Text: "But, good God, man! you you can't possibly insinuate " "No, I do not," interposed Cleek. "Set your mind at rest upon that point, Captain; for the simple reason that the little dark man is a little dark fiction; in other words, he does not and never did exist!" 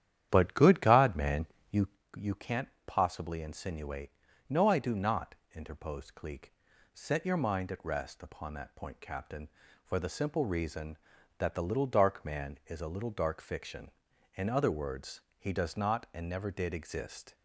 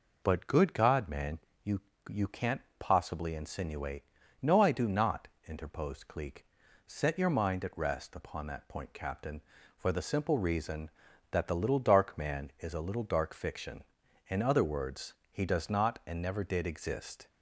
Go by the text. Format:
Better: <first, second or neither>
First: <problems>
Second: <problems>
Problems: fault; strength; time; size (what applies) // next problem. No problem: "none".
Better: second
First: starts louder than the rest; strong; until 2.1 s; 10.5 dB // pauses between "you" and "you"; slight; at 1.8 s; 0.28 s long // pauses between "can't" and "possibly"; slight; at 2.6 s; 0.20 s long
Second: pauses between "you" and "you"; slight; at 1.8 s; 0.28 s long // pauses between "can't" and "possibly"; slight; at 2.6 s; 0.20 s long